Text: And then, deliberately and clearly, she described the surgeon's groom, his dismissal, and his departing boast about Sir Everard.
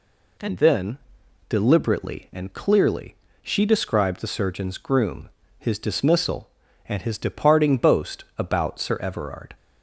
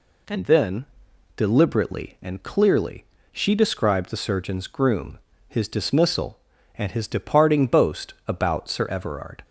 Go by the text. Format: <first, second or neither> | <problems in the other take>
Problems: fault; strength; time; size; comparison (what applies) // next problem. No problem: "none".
neither | none